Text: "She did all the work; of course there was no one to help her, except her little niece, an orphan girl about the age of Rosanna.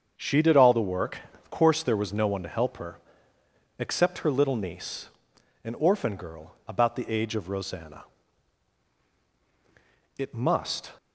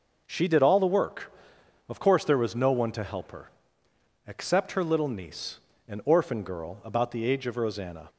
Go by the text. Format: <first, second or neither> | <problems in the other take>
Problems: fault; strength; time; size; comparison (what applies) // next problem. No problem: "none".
second | starts louder than the rest; until 1.1 s; 7 dB // goes on to say "It must"; noticeable; from 10.1 s on; 0.74 s long